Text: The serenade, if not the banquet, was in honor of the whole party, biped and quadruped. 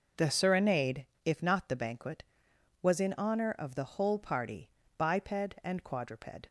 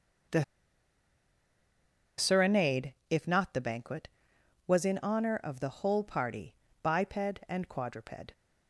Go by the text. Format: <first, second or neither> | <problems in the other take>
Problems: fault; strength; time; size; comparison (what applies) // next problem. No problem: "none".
first | pauses between "The" and "serenade"; strong; at 0.4 s; 1.7 s long